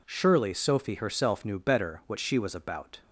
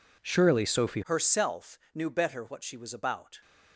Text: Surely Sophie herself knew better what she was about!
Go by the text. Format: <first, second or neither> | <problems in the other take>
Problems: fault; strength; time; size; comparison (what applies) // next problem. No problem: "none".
first | changes voice at "herself"; from 1.0 s on; 2.4 s long